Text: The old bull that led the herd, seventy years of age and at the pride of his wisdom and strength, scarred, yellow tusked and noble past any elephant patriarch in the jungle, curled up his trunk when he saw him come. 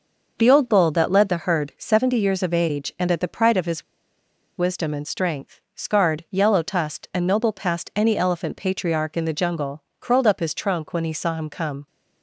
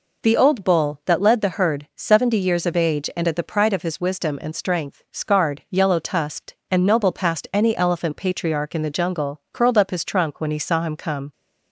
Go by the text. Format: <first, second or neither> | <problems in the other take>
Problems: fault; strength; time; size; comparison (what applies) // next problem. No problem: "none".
second | pauses between "his" and "wisdom"; noticeable; at 3.8 s; 0.74 s long